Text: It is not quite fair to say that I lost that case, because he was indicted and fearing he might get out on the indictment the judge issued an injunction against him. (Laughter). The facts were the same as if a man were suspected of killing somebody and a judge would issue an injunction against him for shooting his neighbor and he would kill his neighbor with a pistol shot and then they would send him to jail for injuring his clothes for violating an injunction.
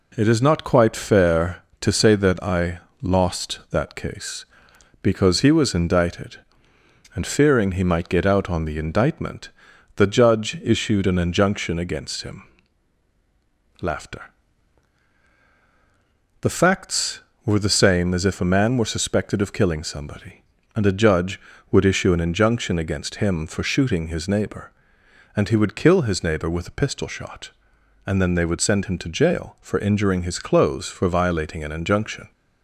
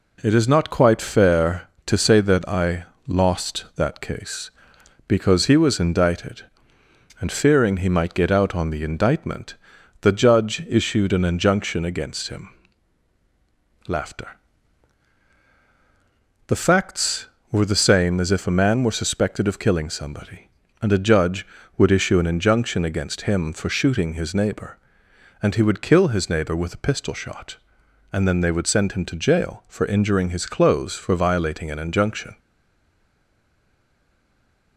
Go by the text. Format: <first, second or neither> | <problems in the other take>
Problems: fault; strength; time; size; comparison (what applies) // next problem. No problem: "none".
first | pauses between "I" and "lost"; slight; at 2.8 s; 0.20 s long; slight in the first // pauses between "indictment" and "the"; noticeable; at 9.5 s; 0.46 s long; noticeable in the first // stays silent after the last word; from 32.3 s on; 2.4 s long